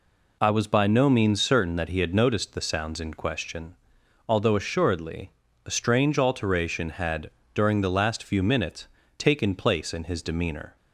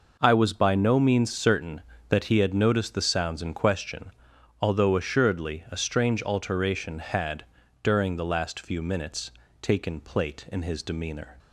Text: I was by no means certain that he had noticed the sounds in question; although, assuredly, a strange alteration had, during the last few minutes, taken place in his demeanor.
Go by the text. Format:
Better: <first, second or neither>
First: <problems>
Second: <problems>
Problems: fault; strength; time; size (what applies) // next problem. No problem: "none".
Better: first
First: none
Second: says "plate" for "place"; at 9.9 s